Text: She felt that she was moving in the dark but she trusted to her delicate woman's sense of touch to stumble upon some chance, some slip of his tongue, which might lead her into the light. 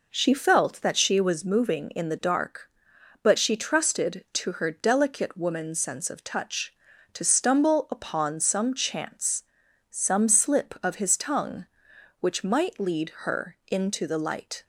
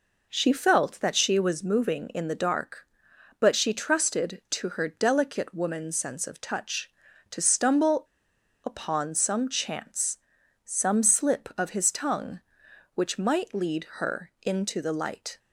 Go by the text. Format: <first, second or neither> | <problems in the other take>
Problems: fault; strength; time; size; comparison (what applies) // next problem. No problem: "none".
first | pauses between "stumble" and "upon"; noticeable; at 8.0 s; 0.61 s long